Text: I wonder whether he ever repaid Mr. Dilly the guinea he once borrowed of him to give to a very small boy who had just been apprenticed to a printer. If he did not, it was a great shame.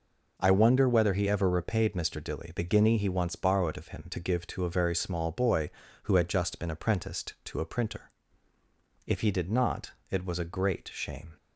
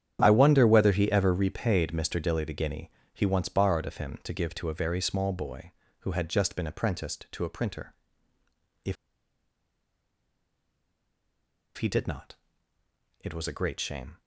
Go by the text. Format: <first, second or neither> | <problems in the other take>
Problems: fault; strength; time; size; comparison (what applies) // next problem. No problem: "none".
first | starts louder than the rest; strong; until 1.2 s; 9.5 dB // pauses between "guinea" and "he"; slight; at 2.9 s; 0.24 s long // pauses between "If" and "he"; strong; at 8.9 s; 2.8 s long